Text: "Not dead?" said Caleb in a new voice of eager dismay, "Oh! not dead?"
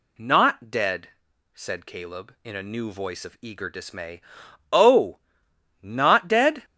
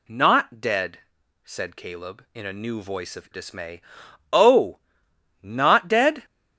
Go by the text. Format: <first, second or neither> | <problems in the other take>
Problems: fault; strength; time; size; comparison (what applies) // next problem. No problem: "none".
first | skips "eager"; at 3.2 s